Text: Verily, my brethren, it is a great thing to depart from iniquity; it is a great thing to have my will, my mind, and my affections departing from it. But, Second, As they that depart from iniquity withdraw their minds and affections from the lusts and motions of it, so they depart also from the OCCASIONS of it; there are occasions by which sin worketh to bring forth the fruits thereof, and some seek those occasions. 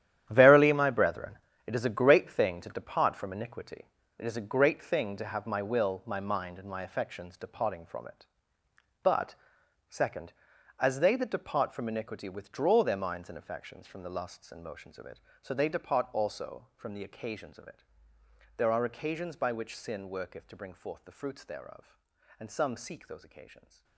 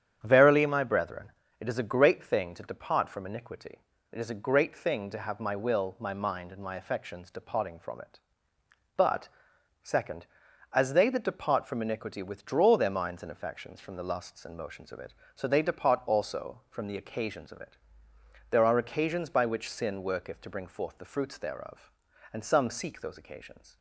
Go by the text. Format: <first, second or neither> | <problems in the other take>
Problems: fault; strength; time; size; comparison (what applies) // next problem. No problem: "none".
second | gets quieter; strong; throughout; 13.5 dB // starts louder than the rest; strong; until 1.3 s; 11 dB; strong in the second